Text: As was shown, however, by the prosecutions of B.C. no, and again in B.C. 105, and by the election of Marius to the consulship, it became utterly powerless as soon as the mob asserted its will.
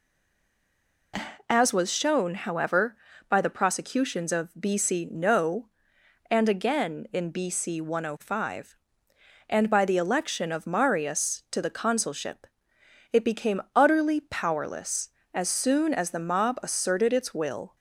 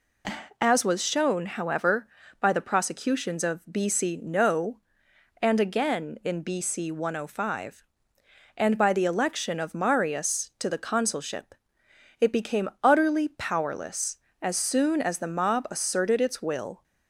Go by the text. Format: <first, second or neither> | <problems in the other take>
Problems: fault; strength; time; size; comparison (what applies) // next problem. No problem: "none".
second | stays silent before the first word; until 1.1 s; 1.1 s long